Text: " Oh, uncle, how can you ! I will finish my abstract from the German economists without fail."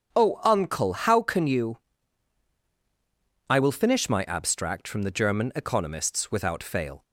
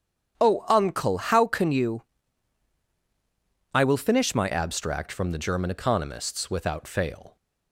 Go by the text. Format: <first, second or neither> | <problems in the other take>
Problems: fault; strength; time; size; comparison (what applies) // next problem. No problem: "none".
first | starts louder than the rest; strong; until 1.3 s; 8.5 dB; strong in the first // changes voice at "abstract"; from 4.5 s on; 2.8 s long